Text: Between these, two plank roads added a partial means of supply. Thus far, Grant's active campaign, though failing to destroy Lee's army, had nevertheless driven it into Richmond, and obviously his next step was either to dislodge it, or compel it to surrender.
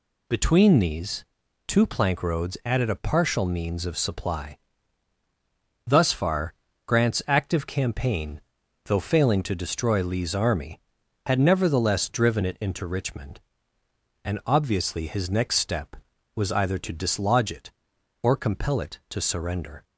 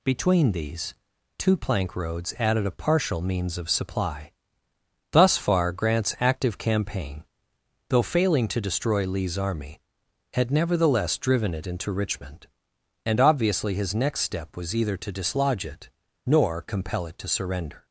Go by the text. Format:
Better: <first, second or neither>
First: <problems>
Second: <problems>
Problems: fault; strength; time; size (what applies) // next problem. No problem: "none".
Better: first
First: none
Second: says "nor" for "or"; at 16.2 s